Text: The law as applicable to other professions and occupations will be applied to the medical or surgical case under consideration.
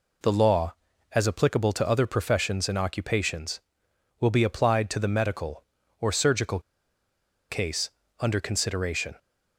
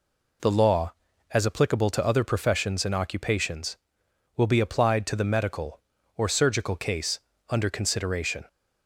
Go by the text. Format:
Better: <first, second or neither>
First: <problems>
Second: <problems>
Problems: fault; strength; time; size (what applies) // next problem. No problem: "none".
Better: second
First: pauses between "surgical" and "case"; noticeable; at 6.5 s; 0.90 s long // pauses between "case" and "under"; slight; at 7.8 s; 0.32 s long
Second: pauses between "case" and "under"; slight; at 7.1 s; 0.32 s long